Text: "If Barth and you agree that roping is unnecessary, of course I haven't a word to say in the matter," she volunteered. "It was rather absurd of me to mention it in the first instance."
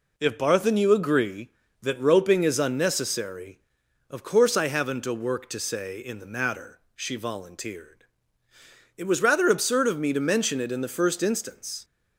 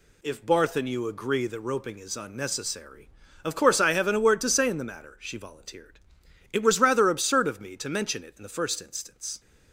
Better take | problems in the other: second | says "work" for "word"; at 5.1 s

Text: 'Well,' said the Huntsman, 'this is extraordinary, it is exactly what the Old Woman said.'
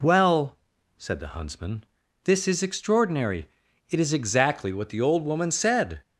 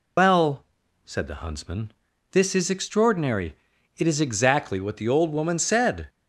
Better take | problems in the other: first | loses the start of "Well"; at 0.1 s; 95 ms

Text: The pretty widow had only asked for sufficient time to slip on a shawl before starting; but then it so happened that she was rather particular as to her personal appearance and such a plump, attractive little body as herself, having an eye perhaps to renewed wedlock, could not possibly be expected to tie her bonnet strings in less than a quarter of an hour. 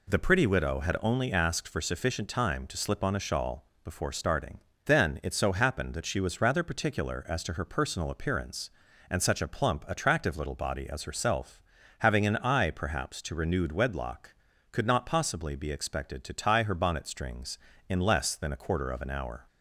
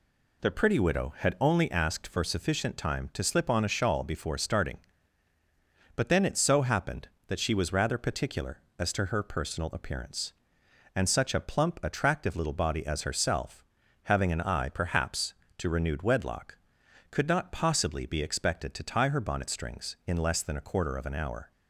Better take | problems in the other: second | pauses between "shawl" and "before"; slight; at 3.6 s; 0.18 s long // skips "but"; at 4.7 s

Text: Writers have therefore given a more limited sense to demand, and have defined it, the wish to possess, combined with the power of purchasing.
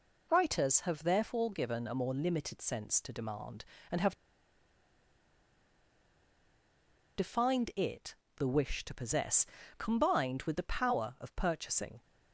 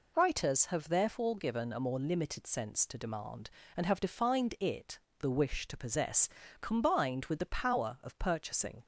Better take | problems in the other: second | pauses between "have" and "defined"; strong; at 4.1 s; 3.0 s long

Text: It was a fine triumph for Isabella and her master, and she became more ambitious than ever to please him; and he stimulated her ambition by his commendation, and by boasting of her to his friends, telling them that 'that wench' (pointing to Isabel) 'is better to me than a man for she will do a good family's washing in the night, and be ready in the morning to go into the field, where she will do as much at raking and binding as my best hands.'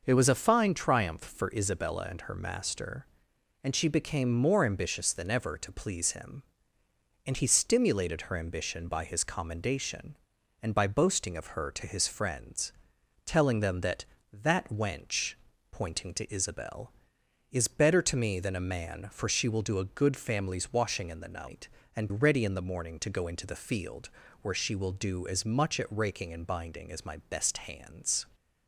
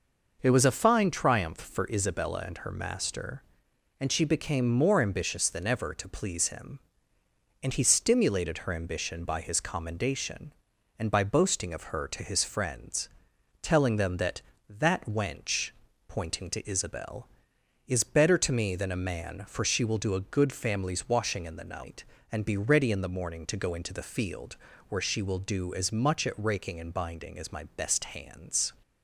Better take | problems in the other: second | skips "be"; at 22.0 s

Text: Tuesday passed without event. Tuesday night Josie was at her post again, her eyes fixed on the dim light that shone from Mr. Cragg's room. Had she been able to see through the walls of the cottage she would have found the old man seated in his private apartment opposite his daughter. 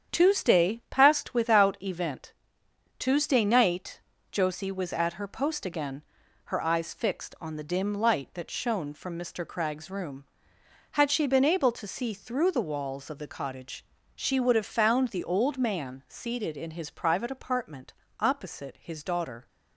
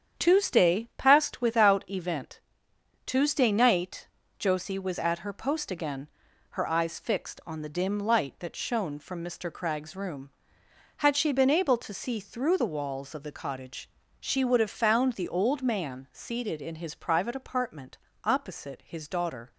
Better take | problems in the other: neither | starts louder than the rest; strong; the same in both // pauses between "night" and "Josie"; slight; the same in both // pauses between "cottage" and "she"; slight; the same in both // pauses between "apartment" and "opposite"; slight; the same in both

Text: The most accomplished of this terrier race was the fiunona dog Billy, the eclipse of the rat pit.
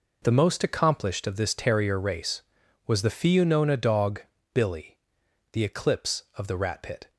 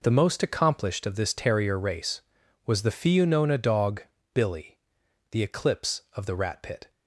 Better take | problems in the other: neither | pauses between "dog" and "Billy"; slight; the same in both

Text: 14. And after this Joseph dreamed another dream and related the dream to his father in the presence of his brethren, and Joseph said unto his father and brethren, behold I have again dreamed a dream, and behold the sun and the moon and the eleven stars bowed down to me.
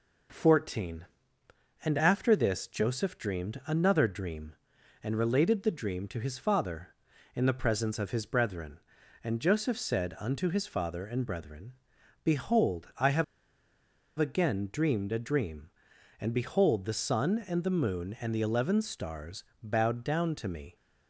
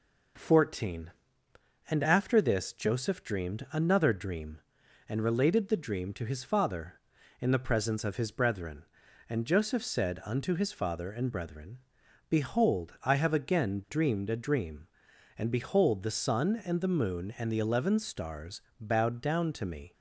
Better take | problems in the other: second | pauses between "have" and "again"; noticeable; at 13.2 s; 0.94 s long // pauses between "stars" and "bowed"; slight; at 19.4 s; 0.18 s long; slight in the second

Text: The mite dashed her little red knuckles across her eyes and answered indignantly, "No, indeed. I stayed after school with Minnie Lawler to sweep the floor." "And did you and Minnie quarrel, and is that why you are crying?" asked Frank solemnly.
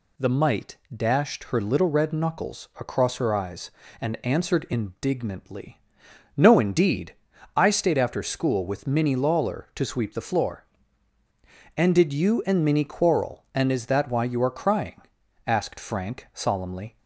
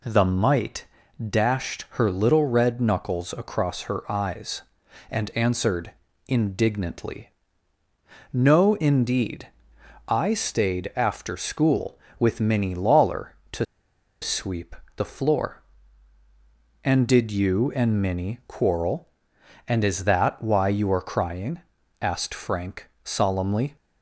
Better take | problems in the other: first | pauses between "mite" and "dashed"; at 0.8 s; 0.44 s long; slight in the first // pauses between "answered" and "indignantly"; slight; at 5.9 s; 0.36 s long // pauses between "to" and "sweep"; noticeable; at 13.6 s; 0.56 s long // pauses between "sweep" and "the"; slight; at 14.7 s; 0.22 s long

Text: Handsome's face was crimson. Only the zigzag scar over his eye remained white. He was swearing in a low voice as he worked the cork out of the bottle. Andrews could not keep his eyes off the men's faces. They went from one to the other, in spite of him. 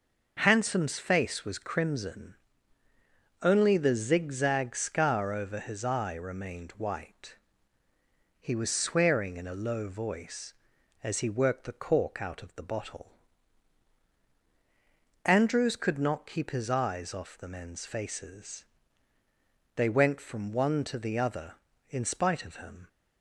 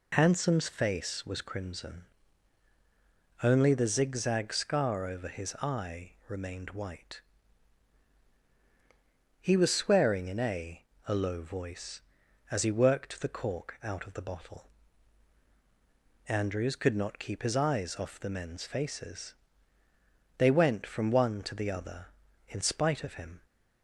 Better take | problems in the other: first | pauses between "eye" and "remained"; slight; at 6.1 s; 0.16 s long // says "a" twice; at 11.0 s

